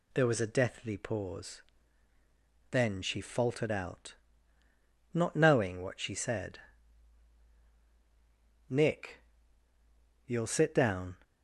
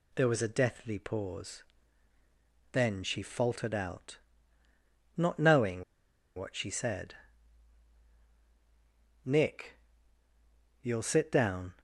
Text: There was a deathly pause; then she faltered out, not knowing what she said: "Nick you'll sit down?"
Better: first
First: pauses between "Nick" and "you'll"; at 9.2 s; 1.0 s long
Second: pauses between "knowing" and "what"; noticeable; at 5.8 s; 0.54 s long // pauses between "Nick" and "you'll"; at 9.7 s; 1.0 s long

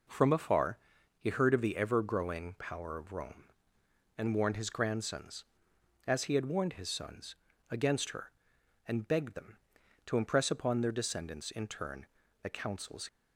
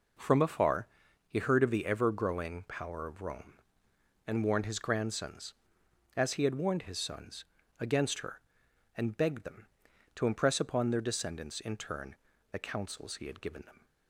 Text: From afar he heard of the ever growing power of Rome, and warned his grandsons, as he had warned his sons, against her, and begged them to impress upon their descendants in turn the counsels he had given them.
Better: second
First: pauses between "afar" and "he"; at 0.7 s; 0.42 s long // pauses between "turn" and "the"; slight; at 12.0 s; 0.36 s long // stops before "he had given them"; at 13.0 s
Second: pauses between "afar" and "he"; at 0.8 s; 0.42 s long // pauses between "turn" and "the"; slight; at 12.1 s; 0.36 s long

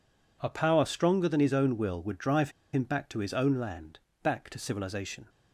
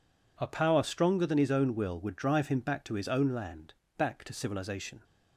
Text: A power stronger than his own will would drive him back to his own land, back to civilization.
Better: second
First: pauses between "drive" and "him"; slight; at 2.4 s; 0.23 s long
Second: none

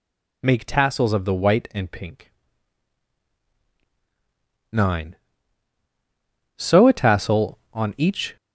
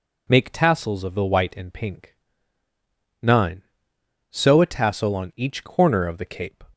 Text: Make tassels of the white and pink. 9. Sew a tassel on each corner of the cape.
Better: second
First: stops before "corner of the cape"; at 8.3 s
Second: none

